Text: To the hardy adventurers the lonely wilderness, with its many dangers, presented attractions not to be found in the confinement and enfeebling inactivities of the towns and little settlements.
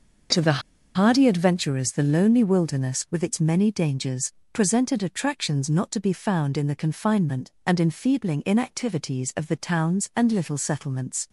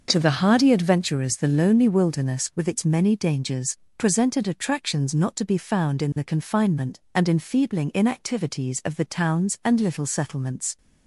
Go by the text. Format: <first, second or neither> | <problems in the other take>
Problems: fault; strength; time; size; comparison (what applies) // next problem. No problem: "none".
second | starts louder than the rest; noticeable; until 1.6 s; 6 dB; also in the second // pauses between "the" and "hardy"; slight; at 0.6 s; 0.34 s long